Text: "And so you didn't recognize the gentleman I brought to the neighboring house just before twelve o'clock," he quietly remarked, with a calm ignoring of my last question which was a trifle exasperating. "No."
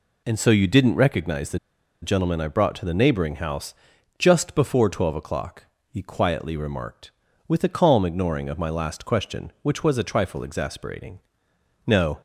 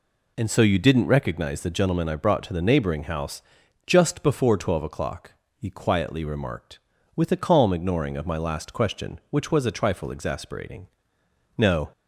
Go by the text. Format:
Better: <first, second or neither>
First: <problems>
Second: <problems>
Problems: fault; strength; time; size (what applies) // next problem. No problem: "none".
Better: second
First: pauses between "the" and "gentleman"; at 1.5 s; 0.44 s long // pauses between "house" and "just"; at 3.7 s; 0.44 s long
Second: pauses between "house" and "just"; at 3.4 s; 0.44 s long